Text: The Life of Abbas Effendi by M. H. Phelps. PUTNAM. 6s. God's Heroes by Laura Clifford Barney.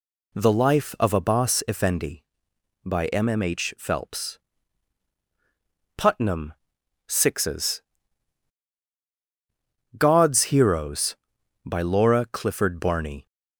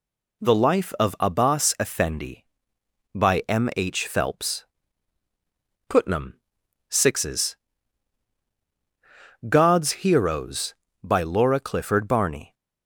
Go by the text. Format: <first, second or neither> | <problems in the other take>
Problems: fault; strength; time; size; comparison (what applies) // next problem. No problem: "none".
second | says "M" twice; at 3.2 s